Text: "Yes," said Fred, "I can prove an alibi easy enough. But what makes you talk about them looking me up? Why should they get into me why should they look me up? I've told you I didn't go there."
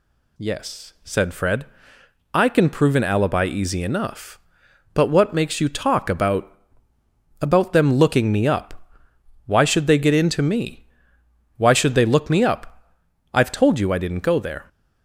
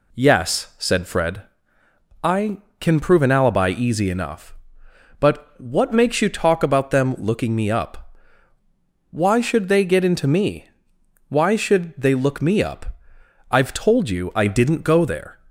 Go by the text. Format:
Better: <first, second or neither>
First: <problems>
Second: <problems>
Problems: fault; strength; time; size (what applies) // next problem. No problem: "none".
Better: second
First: says "about" twice; at 7.4 s // pauses between "me" and "why"; noticeable; at 10.8 s; 0.72 s long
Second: pauses between "me" and "why"; noticeable; at 10.6 s; 0.64 s long